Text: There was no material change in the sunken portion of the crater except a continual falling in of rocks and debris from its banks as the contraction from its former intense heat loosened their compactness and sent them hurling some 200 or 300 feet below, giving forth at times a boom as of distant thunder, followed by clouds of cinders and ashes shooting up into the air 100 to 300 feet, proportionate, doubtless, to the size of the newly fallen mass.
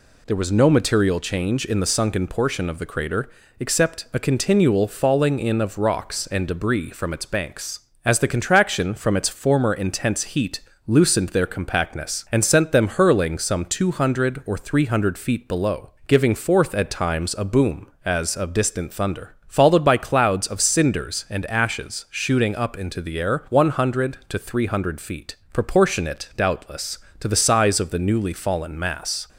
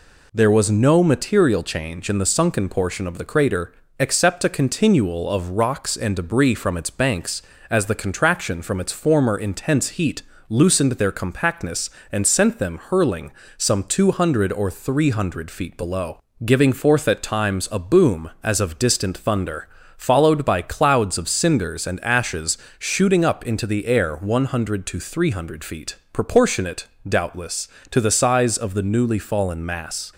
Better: first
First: pauses between "crater" and "except"; slight; at 3.2 s; 0.30 s long // pauses between "heat" and "loosened"; slight; at 10.5 s; 0.26 s long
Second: pauses between "crater" and "except"; slight; at 3.7 s; 0.24 s long // skips "falling in"; at 5.2 s // pauses between "heat" and "loosened"; slight; at 10.2 s; 0.26 s long // pauses between "hurling" and "some"; slight; at 13.3 s; 0.26 s long // pauses between "ashes" and "shooting"; slight; at 22.5 s; 0.22 s long

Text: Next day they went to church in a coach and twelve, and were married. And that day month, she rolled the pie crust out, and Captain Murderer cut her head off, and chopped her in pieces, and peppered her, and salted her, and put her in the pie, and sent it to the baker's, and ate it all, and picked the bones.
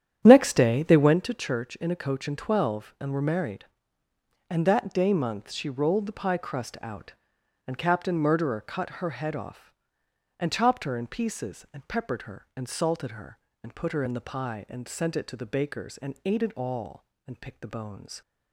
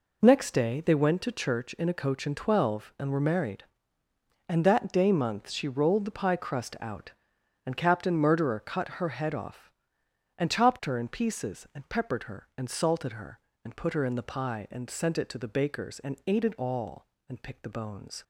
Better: second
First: starts louder than the rest; strong; until 1.4 s; 10 dB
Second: none

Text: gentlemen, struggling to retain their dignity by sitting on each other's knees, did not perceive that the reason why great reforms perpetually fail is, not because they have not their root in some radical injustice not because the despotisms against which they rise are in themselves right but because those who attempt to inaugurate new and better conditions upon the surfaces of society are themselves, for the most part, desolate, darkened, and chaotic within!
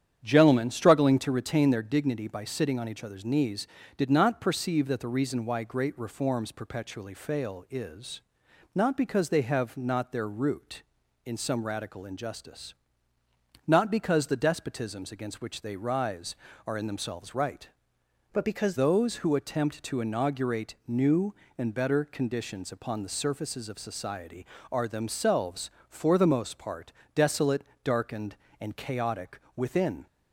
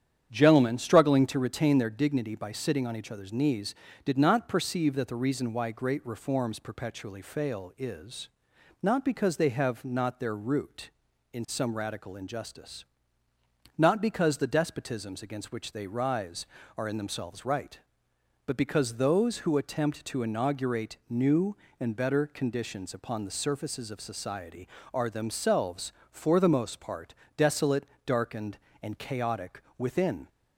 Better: second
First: starts louder than the rest; strong; until 1.2 s; 9 dB // pauses between "injustice" and "not"; noticeable; at 12.7 s; 0.96 s long // changes voice from "but" to "because"; from 18.3 to 18.7 s; 0.4 s long // pauses between "chaotic" and "within"; slight; at 29.3 s; 0.16 s long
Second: starts louder than the rest; strong; until 1.3 s; 9 dB // pauses between "injustice" and "not"; noticeable; at 12.8 s; 0.96 s long // pauses between "chaotic" and "within"; slight; at 29.6 s; 0.16 s long

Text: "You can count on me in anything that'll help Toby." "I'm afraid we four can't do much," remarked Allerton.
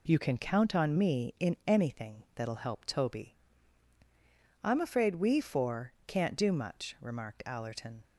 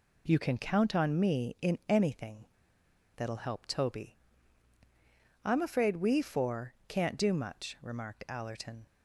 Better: first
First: none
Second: pauses between "anything" and "that'll"; noticeable; at 2.4 s; 0.69 s long

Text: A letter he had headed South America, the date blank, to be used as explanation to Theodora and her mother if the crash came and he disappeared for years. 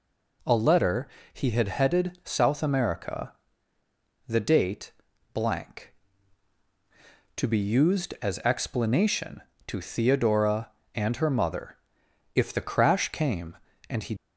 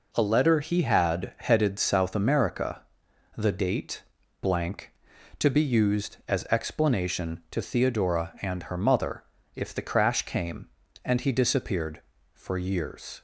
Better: second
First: pauses between "letter" and "he"; slight; at 1.0 s; 0.26 s long // pauses between "date" and "blank"; at 4.9 s; 0.44 s long // pauses between "mother" and "if"; noticeable; at 11.7 s; 0.58 s long // stops before "disappeared for years"; at 14.1 s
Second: pauses between "date" and "blank"; at 4.0 s; 0.40 s long // pauses between "mother" and "if"; slight; at 9.2 s; 0.32 s long

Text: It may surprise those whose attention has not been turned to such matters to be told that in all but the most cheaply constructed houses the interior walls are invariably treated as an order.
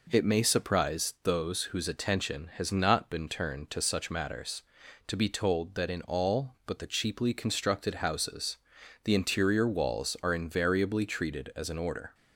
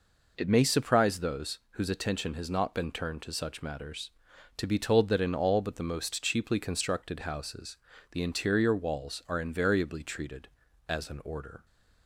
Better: second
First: skips "most"; at 6.8 s // pauses between "houses" and "the"; noticeable; at 8.5 s; 0.48 s long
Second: pauses between "houses" and "the"; slight; at 7.7 s; 0.34 s long

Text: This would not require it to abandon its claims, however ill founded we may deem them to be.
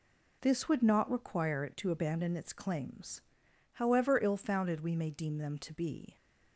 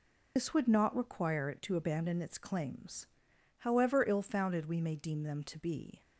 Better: first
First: none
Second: loses the start of "This"; at 0.3 s; 90 ms

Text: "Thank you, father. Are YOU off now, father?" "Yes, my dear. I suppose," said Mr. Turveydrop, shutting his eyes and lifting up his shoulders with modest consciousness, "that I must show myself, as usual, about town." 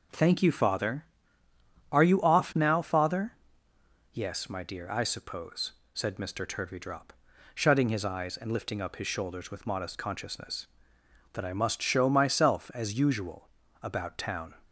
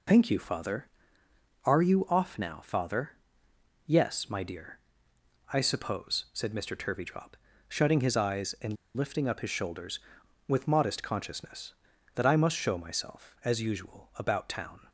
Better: first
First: none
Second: pauses between "and" and "lifting"; slight; at 8.7 s; 0.21 s long

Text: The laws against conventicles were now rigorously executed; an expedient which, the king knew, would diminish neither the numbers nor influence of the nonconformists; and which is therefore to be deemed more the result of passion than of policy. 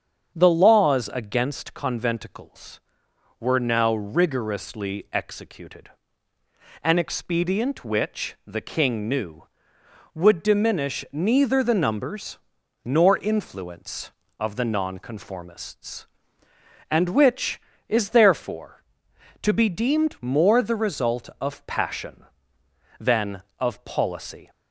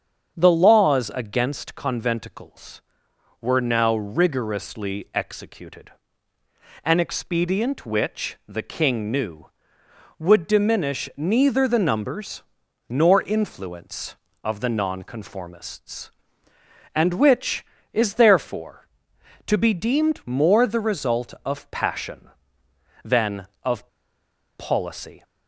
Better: first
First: starts louder than the rest; strong; until 1.3 s; 7.5 dB // pauses between "numbers" and "nor"; noticeable; at 12.3 s; 0.48 s long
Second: starts louder than the rest; strong; until 1.3 s; 7.5 dB // pauses between "numbers" and "nor"; noticeable; at 12.4 s; 0.48 s long // pauses between "of" and "policy"; noticeable; at 23.8 s; 0.72 s long

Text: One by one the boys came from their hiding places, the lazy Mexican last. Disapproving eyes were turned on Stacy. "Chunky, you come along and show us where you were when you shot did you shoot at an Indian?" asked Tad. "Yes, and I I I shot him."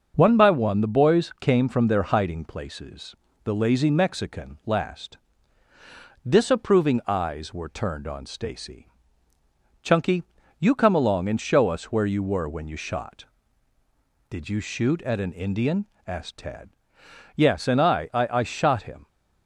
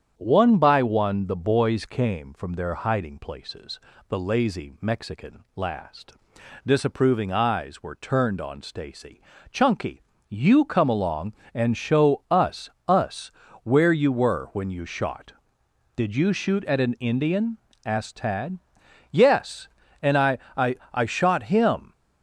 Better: first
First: starts louder than the rest; until 1.1 s; 6 dB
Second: starts louder than the rest; strong; until 1.1 s; 8.5 dB // says "us" twice; at 12.8 s // pauses between "I" and "I"; slight; at 20.3 s; 0.18 s long // pauses between "I" and "I"; slight; at 20.7 s; 0.16 s long

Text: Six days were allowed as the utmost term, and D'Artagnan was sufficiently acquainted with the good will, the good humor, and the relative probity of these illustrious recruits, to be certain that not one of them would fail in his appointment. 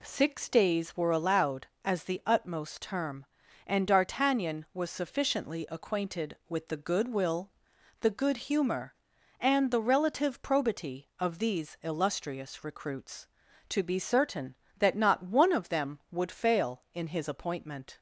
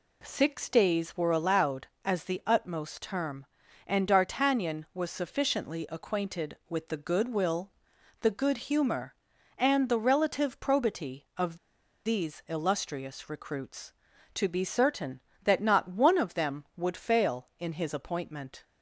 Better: first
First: none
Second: pauses between "of" and "these"; noticeable; at 11.5 s; 0.49 s long

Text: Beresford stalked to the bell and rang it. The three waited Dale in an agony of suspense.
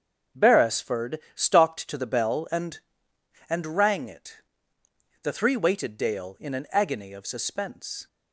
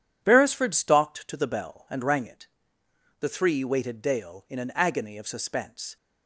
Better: second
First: starts louder than the rest; until 1.5 s; 7 dB // pauses between "Beresford" and "stalked"; slight; at 1.1 s; 0.16 s long // says "and" twice; at 3.4 s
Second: none

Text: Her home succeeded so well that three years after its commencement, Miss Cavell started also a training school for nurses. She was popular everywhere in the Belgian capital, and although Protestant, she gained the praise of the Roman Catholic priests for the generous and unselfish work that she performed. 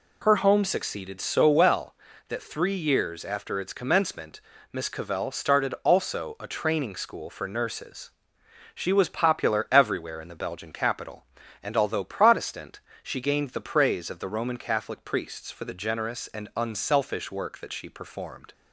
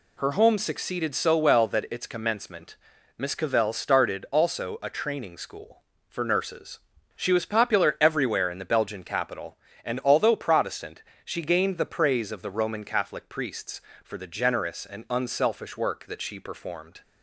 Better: first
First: none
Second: skips "three years after"; at 1.8 s

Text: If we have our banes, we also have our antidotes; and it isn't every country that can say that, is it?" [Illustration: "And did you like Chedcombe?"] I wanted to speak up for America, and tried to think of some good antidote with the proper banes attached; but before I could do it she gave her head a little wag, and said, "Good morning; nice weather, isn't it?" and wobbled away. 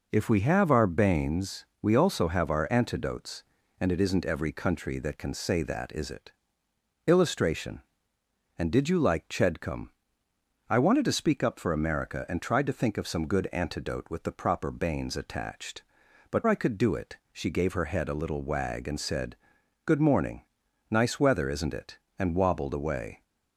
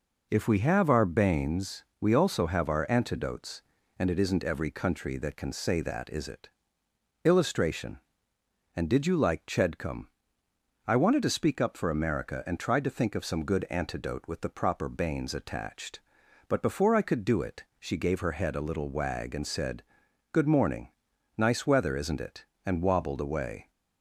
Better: second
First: skips "before"; at 16.4 s // pauses between "it" and "she"; slight; at 17.1 s; 0.16 s long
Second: pauses between "it" and "she"; slight; at 17.6 s; 0.16 s long

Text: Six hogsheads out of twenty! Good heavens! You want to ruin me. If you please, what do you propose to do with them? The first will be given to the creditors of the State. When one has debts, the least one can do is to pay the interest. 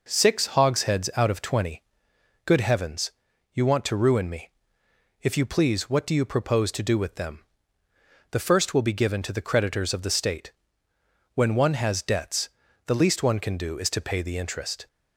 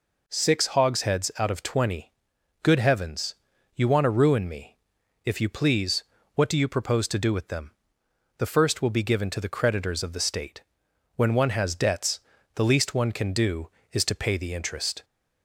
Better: neither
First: none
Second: none

